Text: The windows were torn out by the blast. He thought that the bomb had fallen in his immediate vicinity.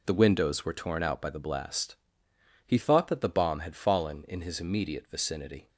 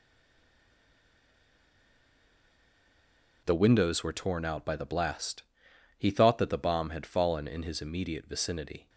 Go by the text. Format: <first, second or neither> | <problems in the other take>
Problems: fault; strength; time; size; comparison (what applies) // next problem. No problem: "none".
first | stays silent before the first word; strong; until 3.4 s; 3.4 s long